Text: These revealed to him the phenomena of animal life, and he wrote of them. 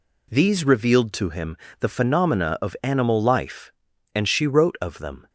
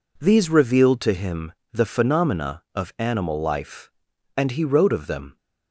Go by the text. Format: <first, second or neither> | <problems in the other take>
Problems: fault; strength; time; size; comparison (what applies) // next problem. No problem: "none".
second | pauses between "him" and "the"; slight; at 1.5 s; 0.22 s long; slight in the second // says "she" for "he"; at 4.2 s